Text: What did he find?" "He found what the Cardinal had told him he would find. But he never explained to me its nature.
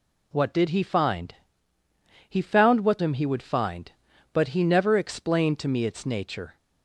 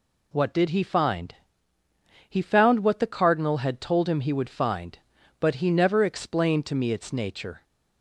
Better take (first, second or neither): second